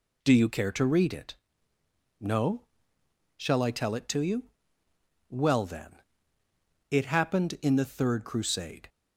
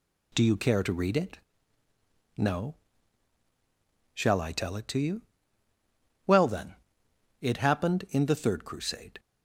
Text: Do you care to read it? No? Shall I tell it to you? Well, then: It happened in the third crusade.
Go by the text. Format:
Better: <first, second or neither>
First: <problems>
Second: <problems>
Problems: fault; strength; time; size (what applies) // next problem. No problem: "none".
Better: neither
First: none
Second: none